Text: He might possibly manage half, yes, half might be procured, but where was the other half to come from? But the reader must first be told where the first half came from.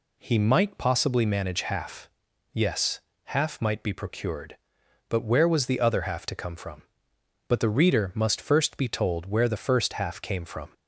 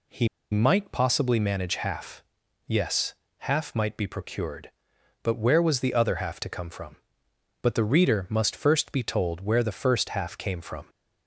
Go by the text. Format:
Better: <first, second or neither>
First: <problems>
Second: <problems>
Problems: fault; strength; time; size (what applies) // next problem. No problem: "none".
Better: first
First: none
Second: pauses between "He" and "might"; slight; at 0.2 s; 0.24 s long